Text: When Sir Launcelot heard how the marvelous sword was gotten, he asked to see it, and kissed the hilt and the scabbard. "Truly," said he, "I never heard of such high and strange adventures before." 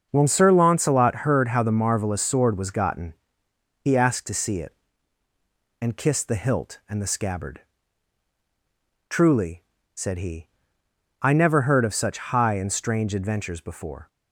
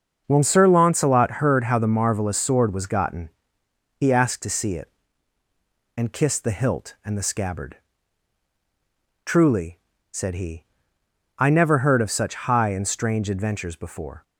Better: neither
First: starts louder than the rest; noticeable; until 1.1 s; 6 dB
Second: starts louder than the rest; noticeable; until 1.2 s; 6 dB

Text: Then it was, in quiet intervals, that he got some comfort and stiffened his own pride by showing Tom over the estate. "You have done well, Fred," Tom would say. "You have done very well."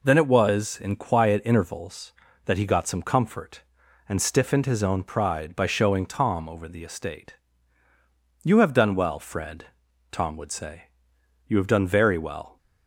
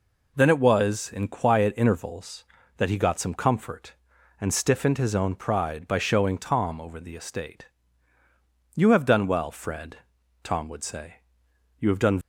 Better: first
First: none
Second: stops before "very well"; at 12.2 s

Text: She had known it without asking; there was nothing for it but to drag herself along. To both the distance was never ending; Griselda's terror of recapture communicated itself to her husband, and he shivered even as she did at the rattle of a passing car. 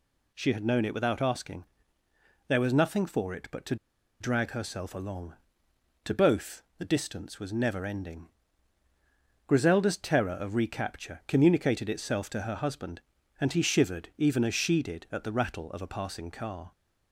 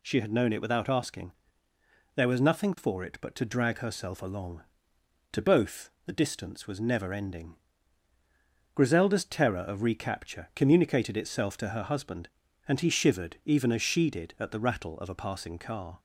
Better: second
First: pauses between "to" and "drag"; at 3.7 s; 0.45 s long // pauses between "both" and "the"; slight; at 6.6 s; 0.16 s long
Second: pauses between "both" and "the"; slight; at 5.8 s; 0.16 s long

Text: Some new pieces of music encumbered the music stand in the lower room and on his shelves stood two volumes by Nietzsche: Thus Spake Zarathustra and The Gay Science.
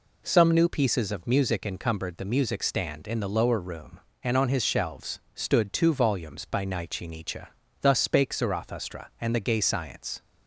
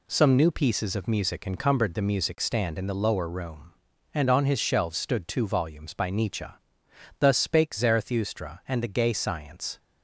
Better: second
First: pauses between "shelves" and "stood"; slight; at 5.1 s; 0.16 s long // says "Nietzsche" twice; at 7.0 s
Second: none

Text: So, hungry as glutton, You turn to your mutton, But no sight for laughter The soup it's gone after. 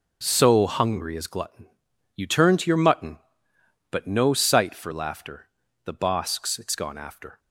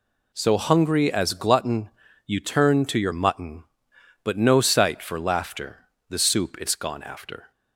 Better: second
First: pauses between "laughter" and "The"; at 5.4 s; 0.38 s long // says "bosks" for "soup"; at 5.9 s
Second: pauses between "laughter" and "The"; slight; at 5.8 s; 0.22 s long

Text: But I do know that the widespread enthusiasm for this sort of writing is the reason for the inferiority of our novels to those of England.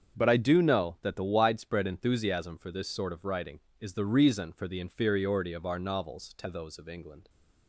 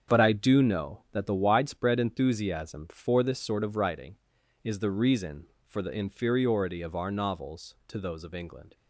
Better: neither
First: starts louder than the rest; strong; until 1.2 s; 7 dB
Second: starts louder than the rest; strong; until 1.1 s; 7.5 dB

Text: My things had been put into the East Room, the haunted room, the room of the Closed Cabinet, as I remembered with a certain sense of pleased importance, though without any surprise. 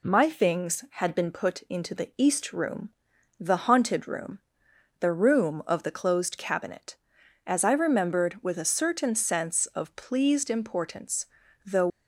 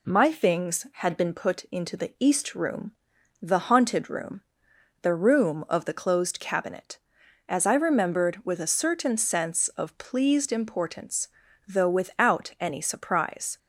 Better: second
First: stops before "without any surprise"; at 11.8 s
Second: none

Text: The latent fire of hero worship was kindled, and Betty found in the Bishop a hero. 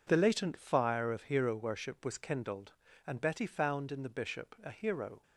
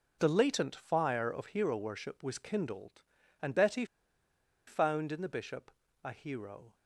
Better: first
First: none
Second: pauses between "Betty" and "found"; noticeable; at 3.8 s; 0.82 s long // pauses between "Bishop" and "a"; slight; at 5.7 s; 0.32 s long

